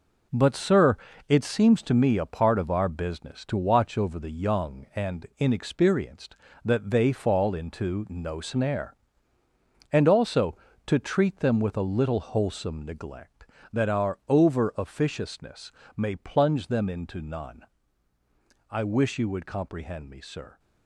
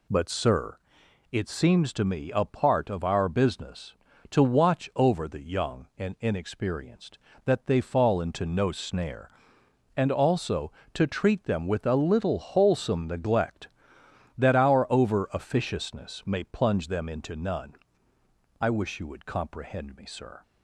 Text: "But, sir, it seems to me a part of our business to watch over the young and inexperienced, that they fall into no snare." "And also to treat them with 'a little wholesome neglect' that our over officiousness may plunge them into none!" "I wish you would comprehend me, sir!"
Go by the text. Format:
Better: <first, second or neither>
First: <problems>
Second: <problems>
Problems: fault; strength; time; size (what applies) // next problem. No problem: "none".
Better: second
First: gets quieter; strong; throughout; 7.5 dB // pauses between "officiousness" and "may"; slight; at 15.7 s; 0.26 s long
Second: none